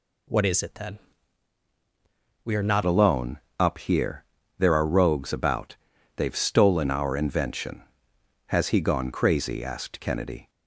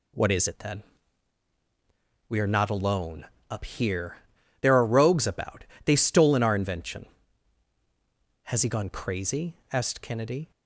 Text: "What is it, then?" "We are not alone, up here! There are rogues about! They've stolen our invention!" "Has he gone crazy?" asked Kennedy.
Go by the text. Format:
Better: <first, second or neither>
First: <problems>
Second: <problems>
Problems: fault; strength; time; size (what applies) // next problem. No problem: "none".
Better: second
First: changes voice at "alone"; from 2.8 s on; 7.6 s long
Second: none